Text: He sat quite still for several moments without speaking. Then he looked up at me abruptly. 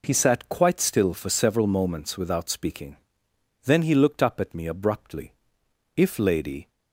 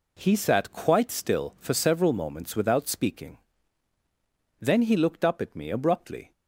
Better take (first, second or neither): second